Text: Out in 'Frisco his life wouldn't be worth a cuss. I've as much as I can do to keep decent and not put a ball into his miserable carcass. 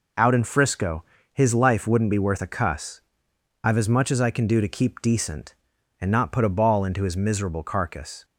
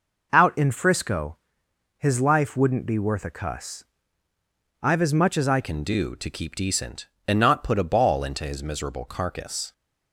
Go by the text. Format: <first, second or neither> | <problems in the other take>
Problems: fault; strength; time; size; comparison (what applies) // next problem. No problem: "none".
first | pauses between "Frisco" and "his"; noticeable; at 1.3 s; 0.60 s long; slight in the first // changes voice at "can"; from 5.6 s on; 4.1 s long